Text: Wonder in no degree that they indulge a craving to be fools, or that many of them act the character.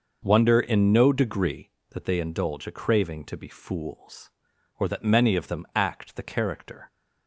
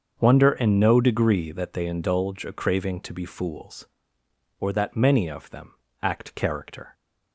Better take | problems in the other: first | starts louder than the rest; until 1.2 s; 7 dB; noticeable in the first // pauses between "them" and "act"; slight; at 5.7 s; 0.26 s long // skips "the"; at 6.3 s

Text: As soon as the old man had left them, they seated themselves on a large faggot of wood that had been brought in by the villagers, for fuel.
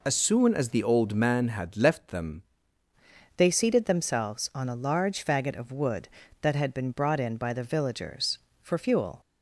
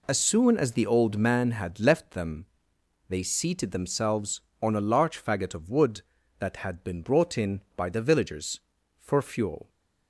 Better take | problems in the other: second | changes voice at "they"; from 3.3 s on; 5.9 s long

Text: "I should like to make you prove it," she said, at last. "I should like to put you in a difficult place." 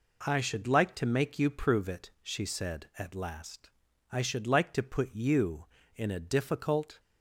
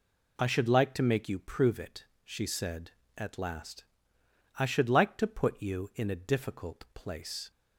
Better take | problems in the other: second | stops before "place"; at 6.9 s

